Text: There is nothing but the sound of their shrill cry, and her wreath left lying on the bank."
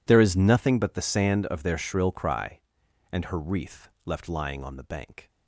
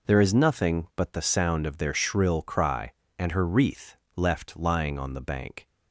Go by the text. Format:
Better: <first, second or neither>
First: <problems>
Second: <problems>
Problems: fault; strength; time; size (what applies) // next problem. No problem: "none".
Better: second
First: says "sand" for "sound"; at 1.0 s // pauses between "wreath" and "left"; slight; at 3.8 s; 0.16 s long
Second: pauses between "wreath" and "left"; slight; at 3.9 s; 0.18 s long